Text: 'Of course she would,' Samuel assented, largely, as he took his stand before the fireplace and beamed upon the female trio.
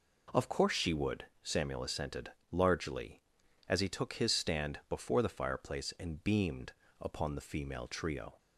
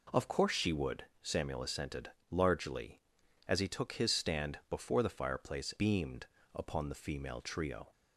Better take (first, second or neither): first